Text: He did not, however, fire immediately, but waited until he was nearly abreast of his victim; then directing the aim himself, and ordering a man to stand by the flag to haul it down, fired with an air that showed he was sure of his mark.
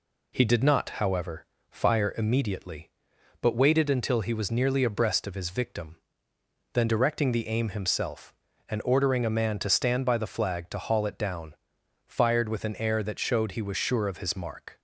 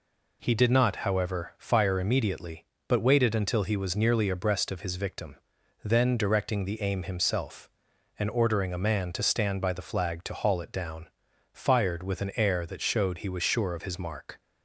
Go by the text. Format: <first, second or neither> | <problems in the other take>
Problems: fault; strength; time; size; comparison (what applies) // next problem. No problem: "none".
neither | none